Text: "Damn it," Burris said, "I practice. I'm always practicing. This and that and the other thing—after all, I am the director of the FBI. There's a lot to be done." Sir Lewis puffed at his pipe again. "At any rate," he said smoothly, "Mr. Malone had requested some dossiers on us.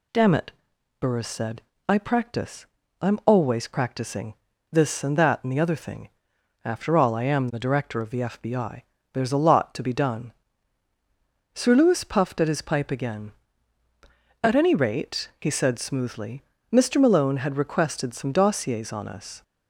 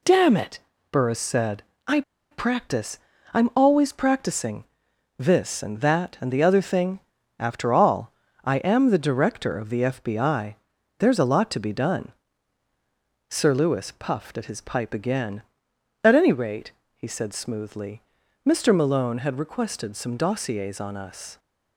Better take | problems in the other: first | pauses between "I" and "practice"; slight; at 2.0 s; 0.29 s long

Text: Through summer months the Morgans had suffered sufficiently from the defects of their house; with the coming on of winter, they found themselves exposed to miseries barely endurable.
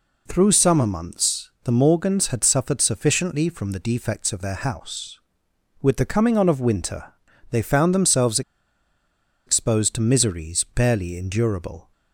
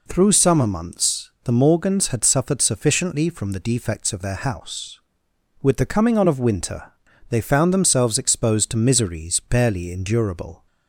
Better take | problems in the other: second | pauses between "themselves" and "exposed"; at 8.4 s; 1.0 s long

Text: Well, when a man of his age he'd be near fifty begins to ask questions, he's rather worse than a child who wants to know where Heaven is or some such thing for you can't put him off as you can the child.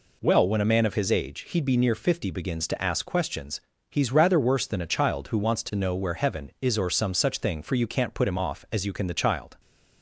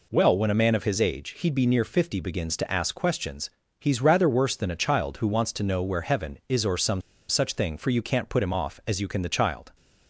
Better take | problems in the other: first | pauses between "some" and "such"; slight; at 7.0 s; 0.28 s long

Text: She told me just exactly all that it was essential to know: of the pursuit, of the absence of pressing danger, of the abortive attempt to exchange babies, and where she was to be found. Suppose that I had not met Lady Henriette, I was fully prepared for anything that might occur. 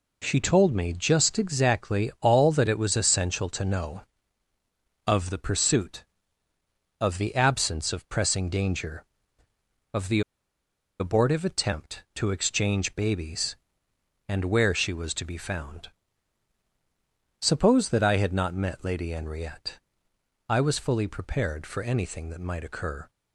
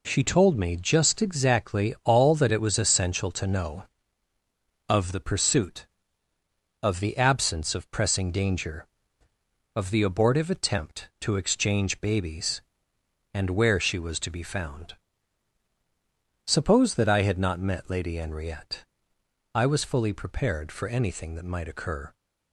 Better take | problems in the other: second | pauses between "the" and "abortive"; noticeable; at 10.2 s; 0.79 s long

